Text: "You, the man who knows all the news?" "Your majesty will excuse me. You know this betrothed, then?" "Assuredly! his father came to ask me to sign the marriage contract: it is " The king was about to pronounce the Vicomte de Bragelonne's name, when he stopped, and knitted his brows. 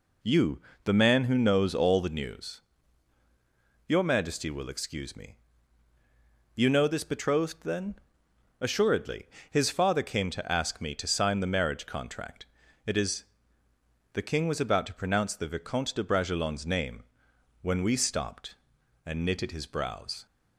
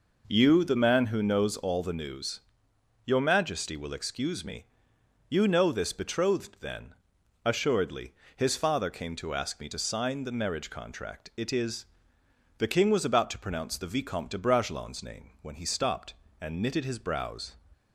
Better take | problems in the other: second | says "we" for "he"; at 17.8 s

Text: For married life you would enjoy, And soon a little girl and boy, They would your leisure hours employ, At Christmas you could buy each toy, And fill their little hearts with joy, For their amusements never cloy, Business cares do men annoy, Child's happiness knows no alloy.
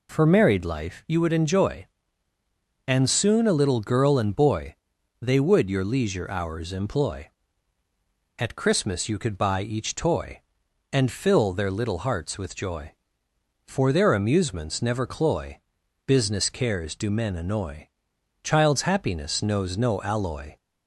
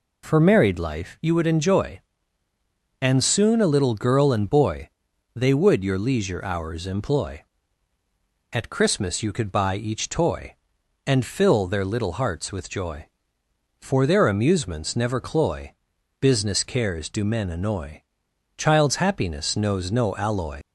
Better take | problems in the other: first | leaves "alloy" unfinished; at 20.6 s; 90 ms

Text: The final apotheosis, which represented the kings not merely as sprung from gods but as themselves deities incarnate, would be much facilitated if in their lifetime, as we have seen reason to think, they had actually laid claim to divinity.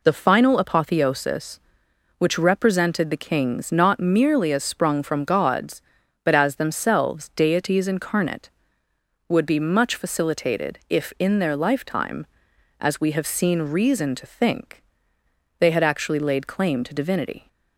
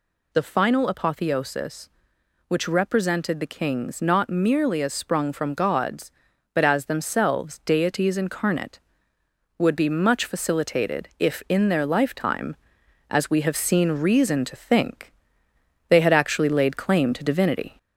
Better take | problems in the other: first | gets louder; slight; throughout; 2 dB

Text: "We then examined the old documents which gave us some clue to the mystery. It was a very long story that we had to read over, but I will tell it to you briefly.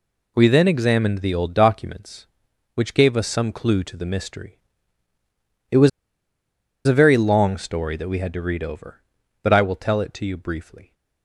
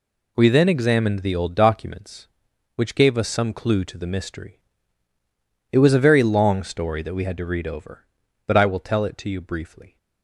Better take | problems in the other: second | pauses between "was" and "a"; noticeable; at 5.8 s; 0.97 s long

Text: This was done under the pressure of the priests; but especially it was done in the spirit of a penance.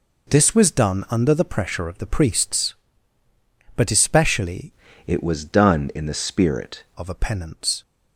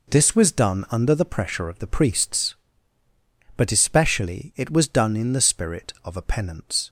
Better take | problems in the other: second | changes voice from "it" to "spirit"; from 5.0 to 6.8 s; 1.8 s long

